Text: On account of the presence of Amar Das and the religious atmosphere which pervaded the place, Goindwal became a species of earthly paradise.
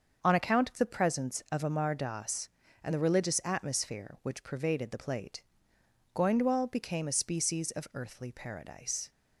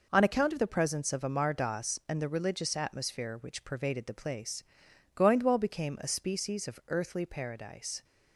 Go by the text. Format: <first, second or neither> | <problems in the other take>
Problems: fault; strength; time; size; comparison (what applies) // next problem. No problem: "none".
second | starts louder than the rest; until 1.2 s; 6.5 dB // says "plate" for "place"; at 4.9 s